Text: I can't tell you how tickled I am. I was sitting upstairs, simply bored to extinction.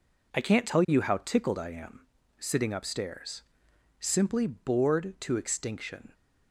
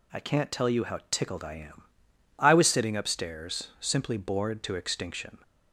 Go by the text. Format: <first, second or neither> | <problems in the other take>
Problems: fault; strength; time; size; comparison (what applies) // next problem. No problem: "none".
second | skips "I was"; at 2.1 s